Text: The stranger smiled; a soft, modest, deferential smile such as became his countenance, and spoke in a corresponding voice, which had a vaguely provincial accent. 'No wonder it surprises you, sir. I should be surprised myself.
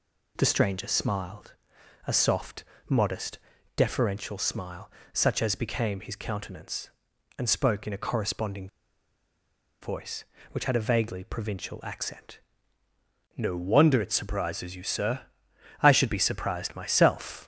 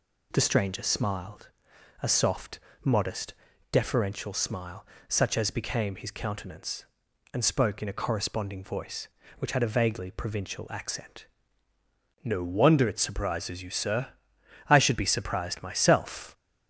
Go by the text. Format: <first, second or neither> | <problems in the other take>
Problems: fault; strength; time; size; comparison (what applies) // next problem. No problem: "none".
second | pauses between "smile" and "such"; slight; at 4.9 s; 0.24 s long; slight in the second // pauses between "corresponding" and "voice"; at 8.6 s; 1.1 s long